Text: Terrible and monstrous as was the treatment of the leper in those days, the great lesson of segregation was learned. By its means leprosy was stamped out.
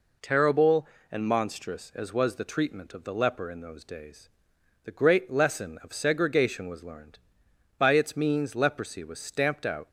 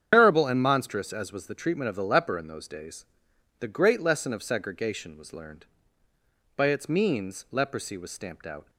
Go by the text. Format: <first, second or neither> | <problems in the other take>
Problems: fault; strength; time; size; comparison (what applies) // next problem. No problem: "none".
first | loses the start of "Terrible"; at 0.1 s; 110 ms // starts louder than the rest; strong; until 1.1 s; 8.5 dB